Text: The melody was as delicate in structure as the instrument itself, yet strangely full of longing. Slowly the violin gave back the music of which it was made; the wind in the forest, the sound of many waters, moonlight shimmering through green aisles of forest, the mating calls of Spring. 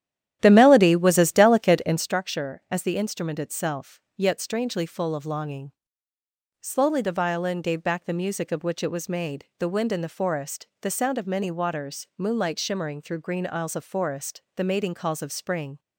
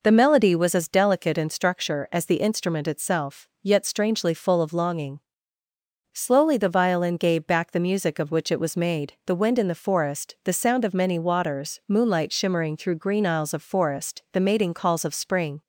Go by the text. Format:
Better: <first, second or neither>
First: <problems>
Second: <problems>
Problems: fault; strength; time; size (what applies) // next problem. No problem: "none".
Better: second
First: starts louder than the rest; strong; until 2.2 s; 11.5 dB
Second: none